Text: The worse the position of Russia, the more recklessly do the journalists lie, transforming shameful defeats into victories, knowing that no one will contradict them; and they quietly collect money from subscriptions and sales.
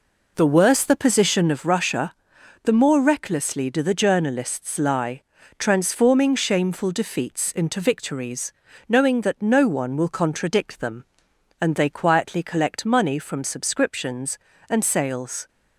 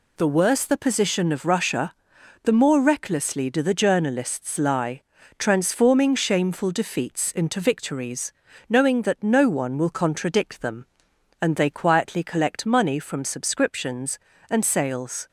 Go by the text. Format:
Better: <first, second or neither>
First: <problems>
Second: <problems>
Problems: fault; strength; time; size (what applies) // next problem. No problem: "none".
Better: second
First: starts louder than the rest; noticeable; until 1.7 s; 4 dB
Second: none